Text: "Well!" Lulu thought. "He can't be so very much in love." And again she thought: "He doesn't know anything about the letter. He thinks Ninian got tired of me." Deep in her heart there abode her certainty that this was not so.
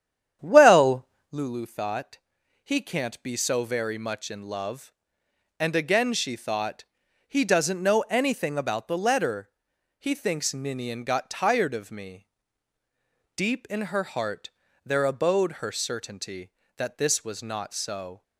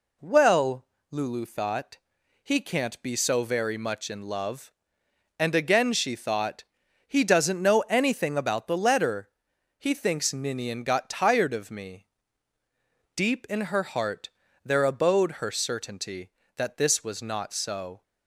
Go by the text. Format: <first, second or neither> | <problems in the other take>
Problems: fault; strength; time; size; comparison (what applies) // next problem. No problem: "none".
second | starts louder than the rest; strong; until 1.4 s; 9.5 dB // pauses between "heart" and "there"; slight; at 14.4 s; 0.36 s long; slight in the second